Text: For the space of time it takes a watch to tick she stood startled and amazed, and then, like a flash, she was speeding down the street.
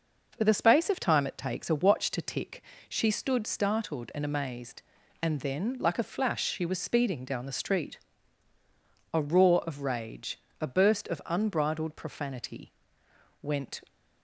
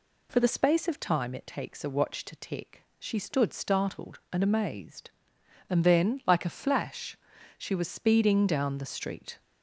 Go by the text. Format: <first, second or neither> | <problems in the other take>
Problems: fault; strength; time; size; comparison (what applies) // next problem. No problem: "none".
second | pauses between "tick" and "she"; slight; at 2.6 s; 0.26 s long; slight in the second // goes on to say "A roar of rage a burst of unbridled profanity went"; strong; from 9.1 s on; 4.6 s long